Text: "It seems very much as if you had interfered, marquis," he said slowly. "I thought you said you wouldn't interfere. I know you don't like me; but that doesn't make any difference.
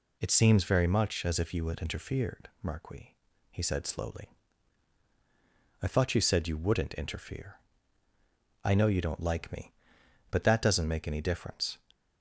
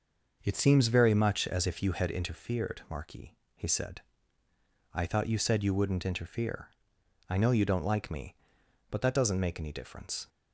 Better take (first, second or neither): first